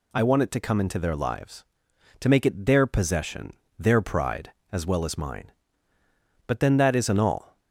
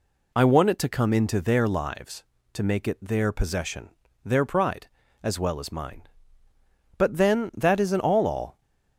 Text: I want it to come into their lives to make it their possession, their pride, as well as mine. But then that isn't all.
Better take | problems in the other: first | says "all" twice; at 8.2 s

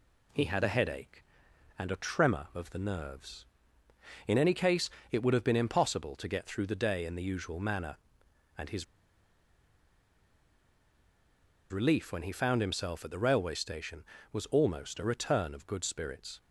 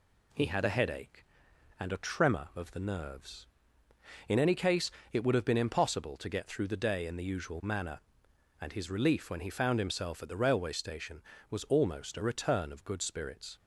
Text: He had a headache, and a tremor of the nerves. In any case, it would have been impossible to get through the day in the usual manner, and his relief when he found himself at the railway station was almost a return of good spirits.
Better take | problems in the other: second | pauses between "his" and "relief"; strong; at 8.8 s; 2.8 s long

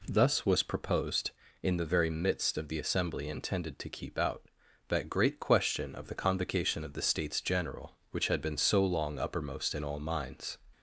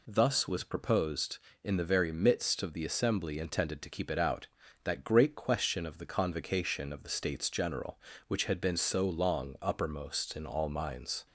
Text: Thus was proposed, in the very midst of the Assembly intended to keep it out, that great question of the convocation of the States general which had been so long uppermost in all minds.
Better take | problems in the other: second | skips "it"; at 4.1 s

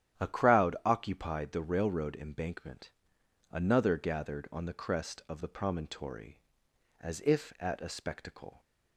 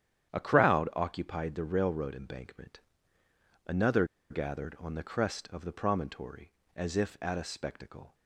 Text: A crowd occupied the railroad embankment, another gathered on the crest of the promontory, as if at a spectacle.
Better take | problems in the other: first | starts louder than the rest; strong; until 1.3 s; 9.5 dB; strong in the first // pauses between "another" and "gathered"; slight; at 4.0 s; 0.25 s long

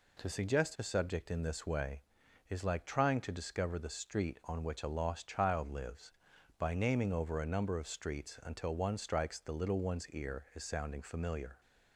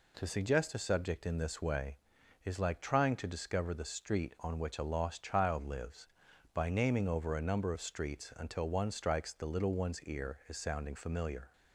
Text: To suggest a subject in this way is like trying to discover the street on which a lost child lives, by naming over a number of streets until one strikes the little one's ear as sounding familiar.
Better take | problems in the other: neither | none

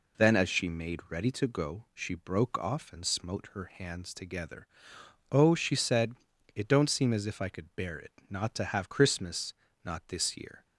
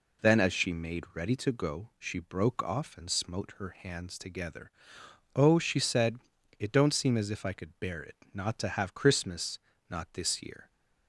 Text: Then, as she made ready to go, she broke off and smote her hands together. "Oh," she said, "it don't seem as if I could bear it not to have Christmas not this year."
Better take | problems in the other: neither | pauses between "it" and "not"; slight; the same in both // pauses between "Christmas" and "not"; slight; the same in both

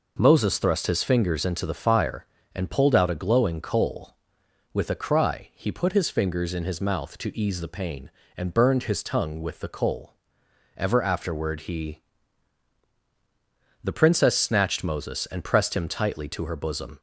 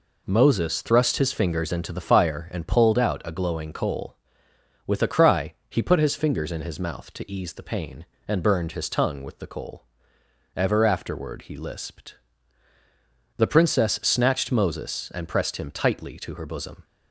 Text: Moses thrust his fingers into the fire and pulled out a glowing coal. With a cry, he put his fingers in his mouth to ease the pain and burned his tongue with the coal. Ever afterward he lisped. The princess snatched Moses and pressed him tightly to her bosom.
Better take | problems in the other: second | skips "lisped"; at 12.9 s

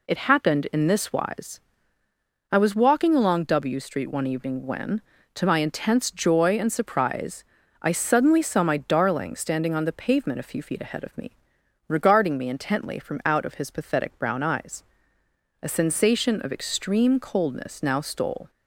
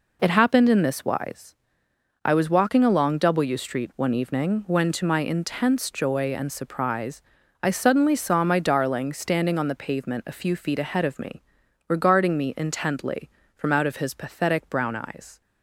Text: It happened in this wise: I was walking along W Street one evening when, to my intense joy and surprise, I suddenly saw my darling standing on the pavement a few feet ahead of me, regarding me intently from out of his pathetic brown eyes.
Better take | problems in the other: second | goes on to say "A sensation of extreme coldness now stole"; strong; from 15.6 s on; 2.8 s long

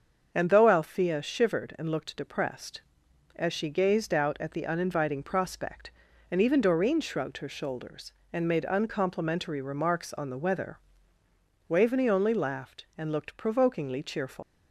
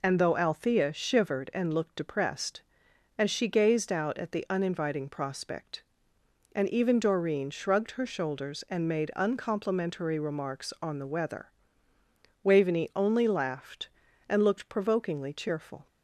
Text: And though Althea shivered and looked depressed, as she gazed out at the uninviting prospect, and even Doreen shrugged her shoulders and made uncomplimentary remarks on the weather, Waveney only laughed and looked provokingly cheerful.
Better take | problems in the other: second | starts louder than the rest; until 1.3 s; 6.5 dB // leaves "cheerful" unfinished; at 14.4 s; 130 ms

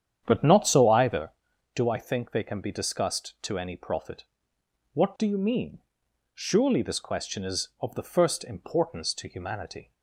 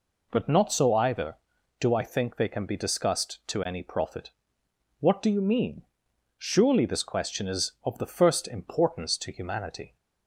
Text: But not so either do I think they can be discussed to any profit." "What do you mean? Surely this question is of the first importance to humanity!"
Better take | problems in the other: second | starts louder than the rest; strong; until 1.4 s; 9 dB

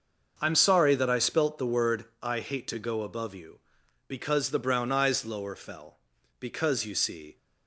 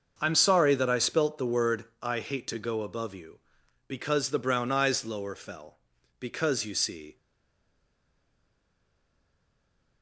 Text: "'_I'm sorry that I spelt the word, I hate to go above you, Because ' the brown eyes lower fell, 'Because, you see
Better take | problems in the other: first | starts louder than the rest; noticeable; until 1.2 s; 6 dB; noticeable in the first // stays silent after the last word; strong; from 7.1 s on; 2.9 s long

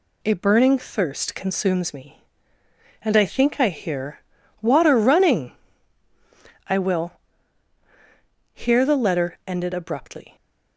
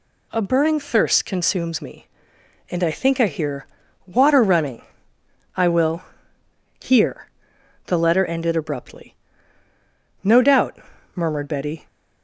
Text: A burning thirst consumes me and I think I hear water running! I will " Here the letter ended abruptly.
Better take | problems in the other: first | pauses between "hear" and "water"; at 3.6 s; 0.40 s long; also in the first // pauses between "Here" and "the"; noticeable; at 7.3 s; 0.56 s long // goes on to say "No doubt murmured Betty"; from 10.2 s on; 1.6 s long

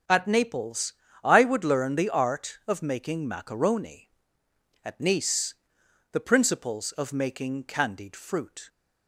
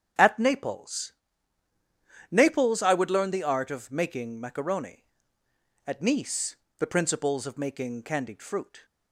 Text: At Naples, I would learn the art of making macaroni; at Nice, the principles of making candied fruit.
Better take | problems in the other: first | starts louder than the rest; strong; until 2.3 s; 8 dB; strong in the first // says "Naples" twice; at 2.3 s

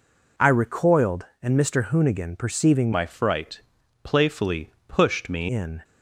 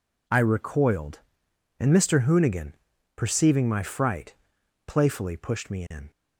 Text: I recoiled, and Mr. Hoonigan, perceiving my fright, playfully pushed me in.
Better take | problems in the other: second | changes voice from "my" to "me"; from 2.9 to 5.4 s; 2.5 s long // pauses between "playfully" and "pushed"; slight; at 4.7 s; 0.16 s long

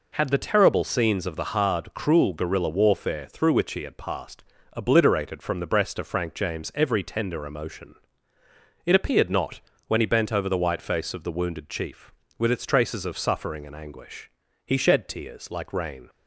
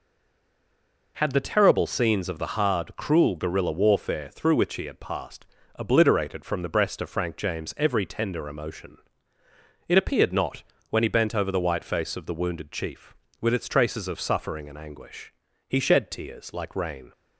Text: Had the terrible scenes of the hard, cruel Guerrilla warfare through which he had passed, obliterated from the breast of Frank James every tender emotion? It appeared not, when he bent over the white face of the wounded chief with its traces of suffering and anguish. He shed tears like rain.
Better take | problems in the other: first | stays silent before the first word; until 1.1 s; 1.1 s long

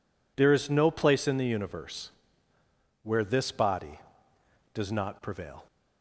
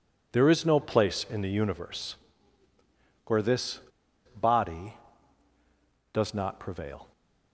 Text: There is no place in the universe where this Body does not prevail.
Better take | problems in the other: first | pauses between "universe" and "where"; at 2.1 s; 1.1 s long; noticeable in the first // pauses between "this" and "Body"; noticeable; at 3.7 s; 0.60 s long

